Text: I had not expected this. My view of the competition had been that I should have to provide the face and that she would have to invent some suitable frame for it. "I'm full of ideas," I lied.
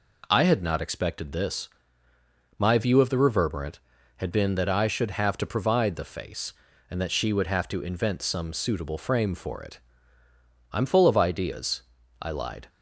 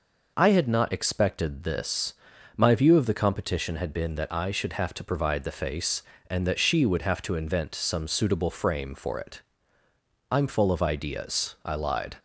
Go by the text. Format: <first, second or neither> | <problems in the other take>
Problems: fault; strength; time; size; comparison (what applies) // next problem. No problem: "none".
second | says "reverberant" for "competition"; at 3.1 s